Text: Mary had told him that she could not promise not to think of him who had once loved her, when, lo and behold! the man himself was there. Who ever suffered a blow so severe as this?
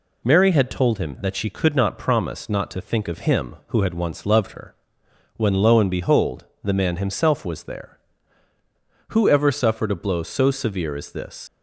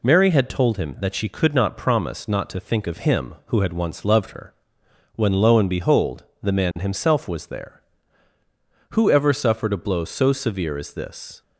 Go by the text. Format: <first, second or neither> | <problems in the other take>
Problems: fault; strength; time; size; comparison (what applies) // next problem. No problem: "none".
second | leaves "this" unfinished; at 11.4 s; 125 ms